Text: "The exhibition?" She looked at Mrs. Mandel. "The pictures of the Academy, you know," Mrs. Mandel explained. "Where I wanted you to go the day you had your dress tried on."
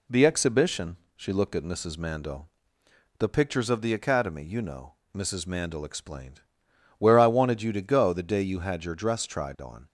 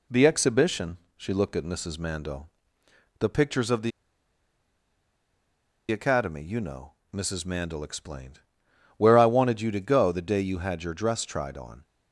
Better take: first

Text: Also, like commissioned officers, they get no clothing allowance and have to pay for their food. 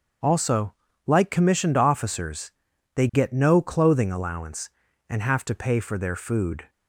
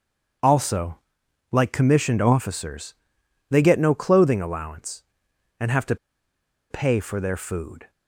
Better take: first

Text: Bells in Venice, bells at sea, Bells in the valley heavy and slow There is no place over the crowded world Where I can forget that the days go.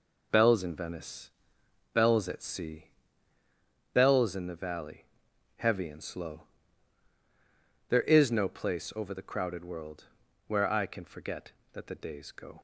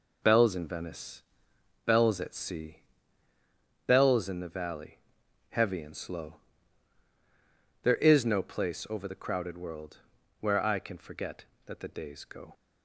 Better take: neither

